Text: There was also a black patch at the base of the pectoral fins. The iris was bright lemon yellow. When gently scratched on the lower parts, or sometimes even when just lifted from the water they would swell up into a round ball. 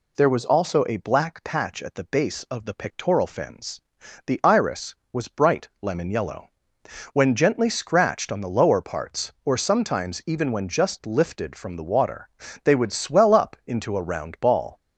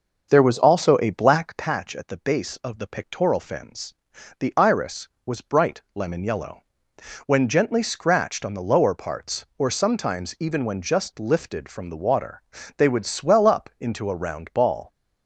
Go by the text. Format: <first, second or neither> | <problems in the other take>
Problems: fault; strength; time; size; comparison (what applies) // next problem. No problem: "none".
first | starts louder than the rest; until 1.7 s; 6 dB // pauses between "water" and "they"; slight; at 12.4 s; 0.34 s long; slight in the first